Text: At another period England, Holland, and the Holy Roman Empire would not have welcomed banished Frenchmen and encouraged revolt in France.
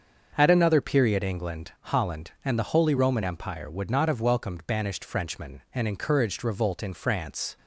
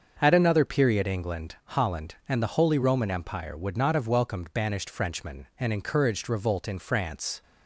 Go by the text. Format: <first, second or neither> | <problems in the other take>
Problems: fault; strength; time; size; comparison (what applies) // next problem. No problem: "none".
neither | starts louder than the rest; the same in both